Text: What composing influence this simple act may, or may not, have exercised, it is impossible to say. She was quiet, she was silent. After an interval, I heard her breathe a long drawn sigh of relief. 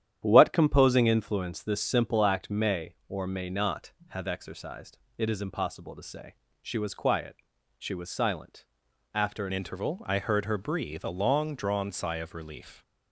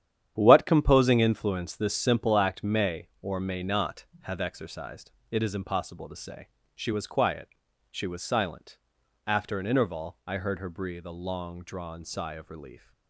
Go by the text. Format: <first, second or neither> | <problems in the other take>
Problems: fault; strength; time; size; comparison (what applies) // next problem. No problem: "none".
second | starts louder than the rest; strong; until 1.2 s; 10.5 dB; strong in the second // changes voice at "interval"; from 9.5 s on; 3.3 s long